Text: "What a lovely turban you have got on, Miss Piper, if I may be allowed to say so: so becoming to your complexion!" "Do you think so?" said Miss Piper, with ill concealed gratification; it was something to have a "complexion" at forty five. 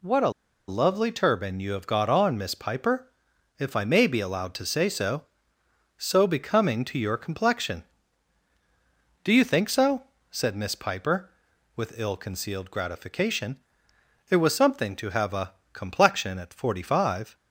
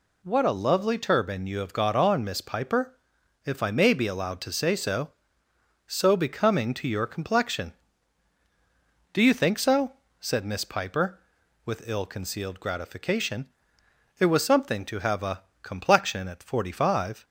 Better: second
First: pauses between "a" and "lovely"; at 0.3 s; 0.36 s long // pauses between "a" and "complexion"; slight; at 15.5 s; 0.18 s long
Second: pauses between "a" and "complexion"; slight; at 15.4 s; 0.18 s long

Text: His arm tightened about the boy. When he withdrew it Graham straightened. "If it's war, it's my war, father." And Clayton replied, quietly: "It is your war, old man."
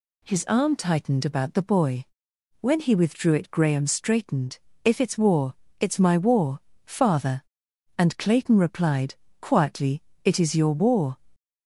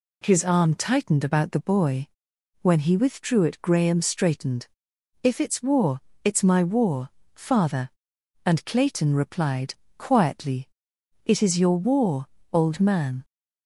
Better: second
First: stops before "old man"; at 11.3 s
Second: none

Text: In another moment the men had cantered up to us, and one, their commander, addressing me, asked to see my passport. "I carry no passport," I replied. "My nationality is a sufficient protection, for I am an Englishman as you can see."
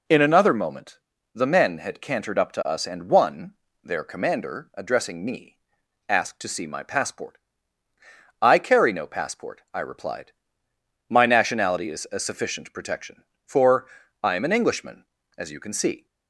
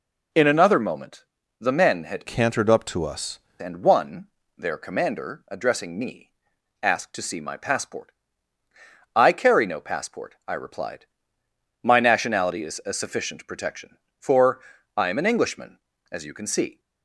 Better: first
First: pauses between "moment" and "the"; slight; at 0.9 s; 0.36 s long // pauses between "for" and "I"; at 13.8 s; 0.38 s long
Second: pauses between "moment" and "the"; slight; at 1.2 s; 0.36 s long // changes voice from "cantered" to "us"; from 2.2 to 3.3 s; 1.1 s long // pauses between "for" and "I"; at 14.5 s; 0.38 s long

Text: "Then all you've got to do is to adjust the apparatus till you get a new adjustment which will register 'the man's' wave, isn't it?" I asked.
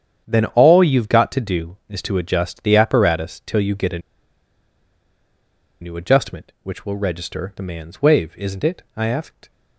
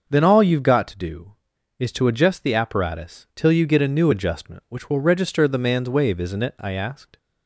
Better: second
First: starts louder than the rest; strong; until 1.2 s; 8.5 dB // pauses between "a" and "new"; strong; at 3.9 s; 1.8 s long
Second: starts louder than the rest; until 1.1 s; 6.5 dB

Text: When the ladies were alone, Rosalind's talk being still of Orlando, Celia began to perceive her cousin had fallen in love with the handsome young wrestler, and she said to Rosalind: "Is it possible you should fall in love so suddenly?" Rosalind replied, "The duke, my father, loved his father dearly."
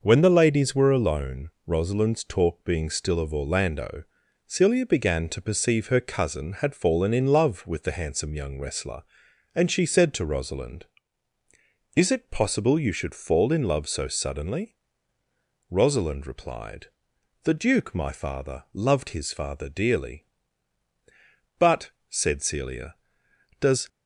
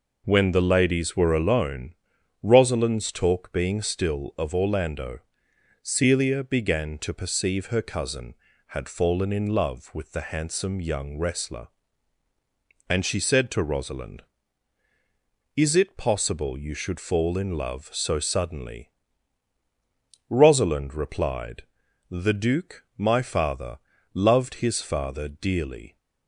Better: second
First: goes on to say "But said Celia does"; strong; from 21.5 s on; 2.2 s long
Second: none

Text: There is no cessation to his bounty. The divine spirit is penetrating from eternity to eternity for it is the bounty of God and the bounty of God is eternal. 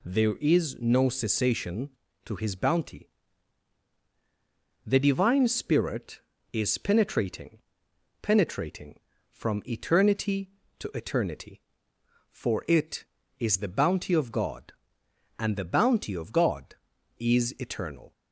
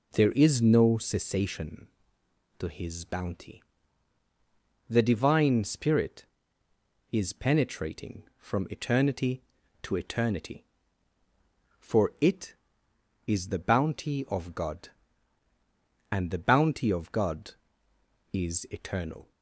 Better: second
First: says "penetrating" twice; at 8.2 s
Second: none

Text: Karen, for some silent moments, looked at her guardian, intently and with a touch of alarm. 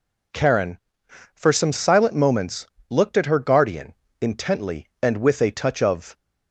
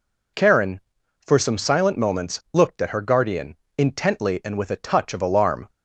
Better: second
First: stops before "alarm"; at 6.1 s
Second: none

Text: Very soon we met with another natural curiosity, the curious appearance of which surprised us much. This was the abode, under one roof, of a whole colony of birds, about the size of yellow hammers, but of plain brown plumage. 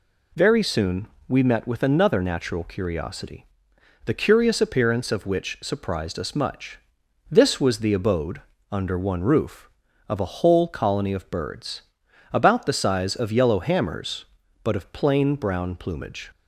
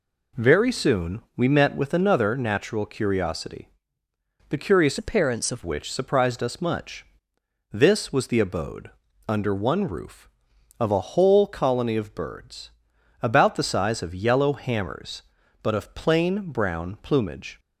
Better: first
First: pauses between "soon" and "we"; slight; at 1.0 s; 0.20 s long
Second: pauses between "soon" and "we"; slight; at 1.2 s; 0.16 s long // changes voice from "appearance" to "of"; from 4.9 to 5.6 s; 0.7 s long

